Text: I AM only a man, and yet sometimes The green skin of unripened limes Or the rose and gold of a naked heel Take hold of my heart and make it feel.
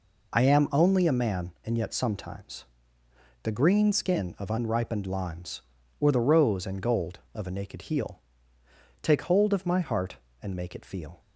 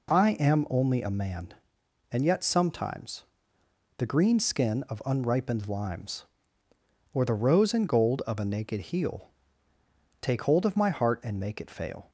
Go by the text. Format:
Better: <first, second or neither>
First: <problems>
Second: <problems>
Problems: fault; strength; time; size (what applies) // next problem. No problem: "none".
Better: first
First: pauses between "sometimes" and "The"; noticeable; at 2.6 s; 0.76 s long // pauses between "heel" and "Take"; noticeable; at 8.1 s; 0.82 s long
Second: pauses between "sometimes" and "The"; noticeable; at 3.2 s; 0.72 s long // pauses between "heel" and "Take"; noticeable; at 9.2 s; 0.90 s long // says "fail" for "feel"; at 11.6 s